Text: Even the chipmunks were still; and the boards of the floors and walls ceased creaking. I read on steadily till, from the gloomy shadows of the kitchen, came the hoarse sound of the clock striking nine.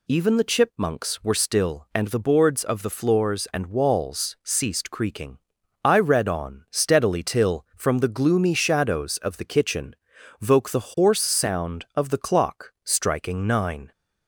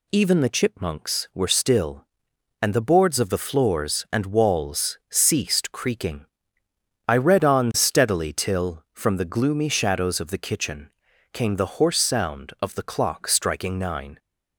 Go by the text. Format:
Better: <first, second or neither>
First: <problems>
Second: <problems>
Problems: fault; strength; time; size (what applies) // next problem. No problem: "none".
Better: second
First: says "voke" for "came"; at 10.4 s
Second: none